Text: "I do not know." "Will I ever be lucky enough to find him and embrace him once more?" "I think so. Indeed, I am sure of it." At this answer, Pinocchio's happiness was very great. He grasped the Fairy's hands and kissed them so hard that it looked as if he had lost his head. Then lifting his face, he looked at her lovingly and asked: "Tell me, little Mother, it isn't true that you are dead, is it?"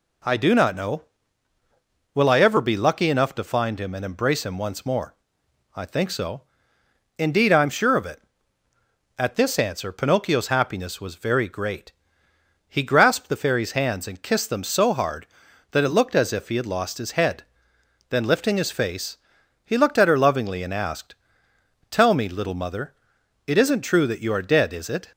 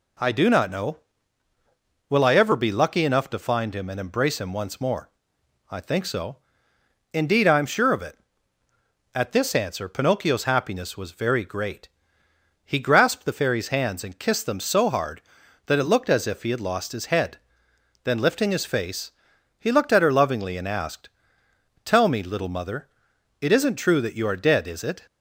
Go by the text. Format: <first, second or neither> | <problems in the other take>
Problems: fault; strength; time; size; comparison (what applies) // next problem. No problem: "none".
neither | none